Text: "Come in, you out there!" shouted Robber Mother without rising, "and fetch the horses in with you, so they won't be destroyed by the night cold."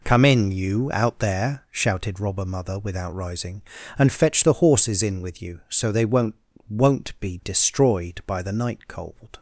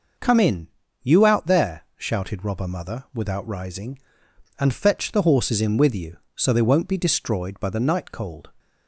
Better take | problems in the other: second | says "won't" twice; at 6.6 s

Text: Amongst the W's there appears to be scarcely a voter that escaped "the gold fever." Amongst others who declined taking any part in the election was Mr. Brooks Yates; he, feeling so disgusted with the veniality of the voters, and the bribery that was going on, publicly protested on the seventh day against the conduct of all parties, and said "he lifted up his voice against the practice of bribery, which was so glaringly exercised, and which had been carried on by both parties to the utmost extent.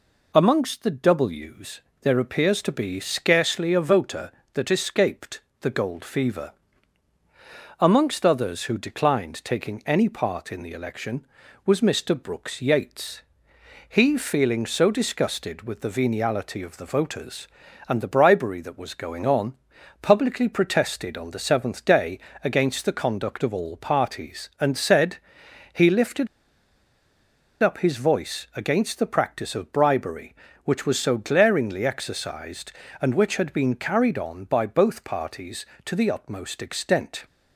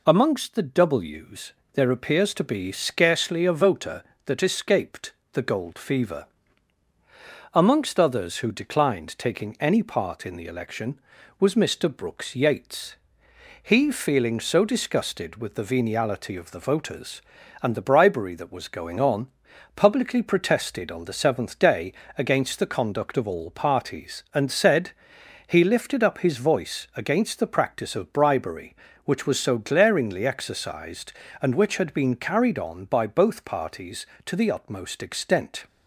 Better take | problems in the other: second | pauses between "W's" and "there"; slight; at 1.8 s; 0.22 s long; slight in the second // pauses between "escaped" and "the"; slight; at 5.4 s; 0.20 s long; slight in the second // pauses between "day" and "against"; slight; at 22.1 s; 0.26 s long; slight in the second // pauses between "said" and "he"; noticeable; at 25.1 s; 0.56 s long; noticeable in the second // pauses between "lifted" and "up"; strong; at 26.2 s; 1.3 s long

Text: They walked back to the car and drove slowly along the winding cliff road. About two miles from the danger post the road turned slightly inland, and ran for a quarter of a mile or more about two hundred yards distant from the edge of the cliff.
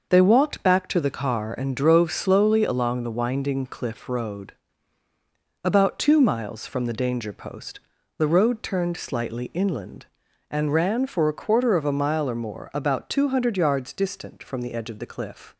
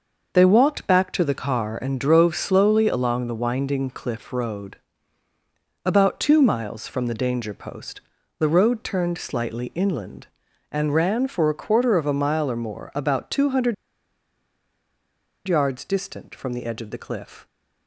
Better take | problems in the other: first | pauses between "post" and "the"; at 7.9 s; 0.38 s long; also in the first // pauses between "hundred" and "yards"; strong; at 13.7 s; 1.7 s long

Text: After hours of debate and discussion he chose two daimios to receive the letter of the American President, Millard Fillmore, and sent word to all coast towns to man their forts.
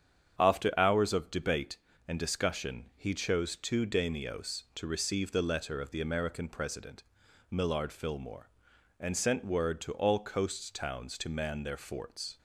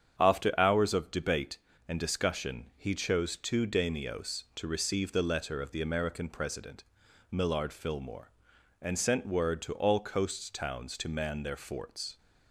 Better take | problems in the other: neither | starts louder than the rest; strong; the same in both

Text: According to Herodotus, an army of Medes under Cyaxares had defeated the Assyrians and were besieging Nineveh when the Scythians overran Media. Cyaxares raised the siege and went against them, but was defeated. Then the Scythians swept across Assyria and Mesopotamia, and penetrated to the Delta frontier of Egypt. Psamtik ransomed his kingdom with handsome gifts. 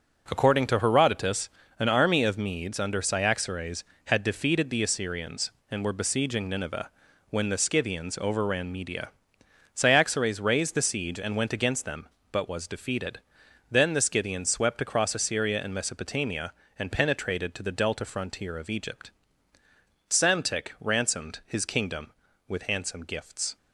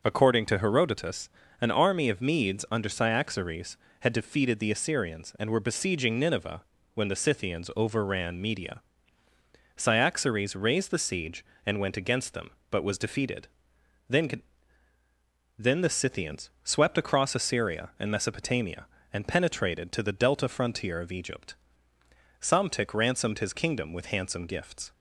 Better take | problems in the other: first | pauses between "Nineveh" and "when"; slight; at 6.6 s; 0.34 s long; also in the first // says "Then" twice; at 15.5 s

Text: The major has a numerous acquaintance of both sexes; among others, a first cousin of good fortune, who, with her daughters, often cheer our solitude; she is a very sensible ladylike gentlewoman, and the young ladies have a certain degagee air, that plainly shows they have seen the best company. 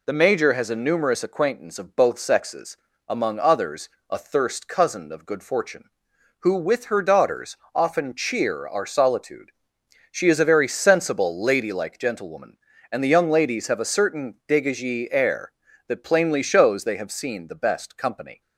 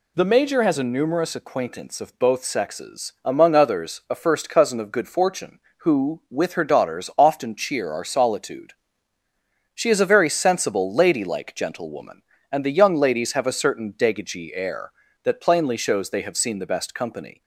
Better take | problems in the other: second | says "thirst" for "first"; at 4.1 s

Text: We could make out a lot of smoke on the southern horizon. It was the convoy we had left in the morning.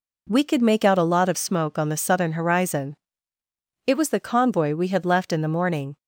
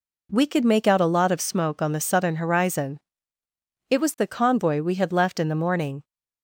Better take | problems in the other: neither | none

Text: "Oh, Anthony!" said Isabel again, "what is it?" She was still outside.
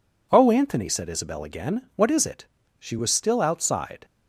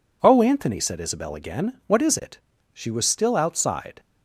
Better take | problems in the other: neither | none

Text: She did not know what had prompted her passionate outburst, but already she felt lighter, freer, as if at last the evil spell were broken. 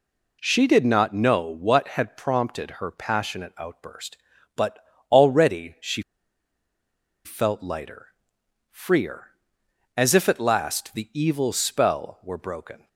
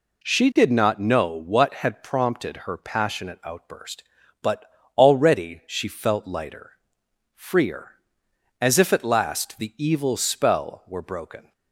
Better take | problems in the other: second | pauses between "but" and "already"; slight; at 4.7 s; 0.32 s long; slight in the second // pauses between "she" and "felt"; at 6.0 s; 1.2 s long

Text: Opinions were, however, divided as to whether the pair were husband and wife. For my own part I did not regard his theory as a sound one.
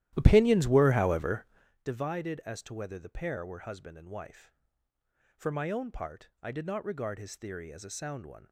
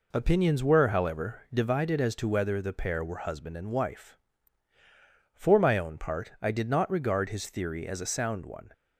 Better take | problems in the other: second | starts louder than the rest; strong; until 1.7 s; 13.5 dB

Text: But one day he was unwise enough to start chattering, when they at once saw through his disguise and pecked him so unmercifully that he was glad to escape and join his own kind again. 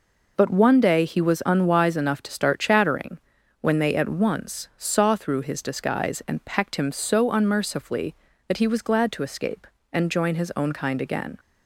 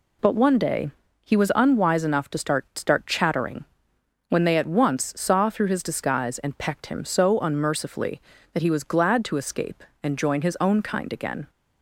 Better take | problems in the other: first | pauses between "day" and "he"; slight; at 0.8 s; 0.33 s long // says "start" twice; at 2.7 s

